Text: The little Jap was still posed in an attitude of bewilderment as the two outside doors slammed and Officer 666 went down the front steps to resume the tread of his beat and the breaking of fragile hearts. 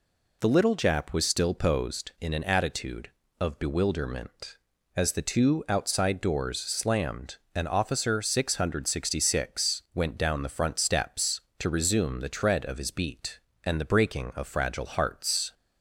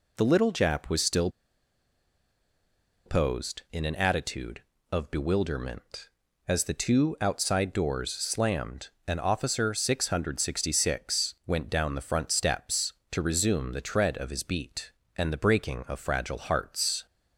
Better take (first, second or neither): first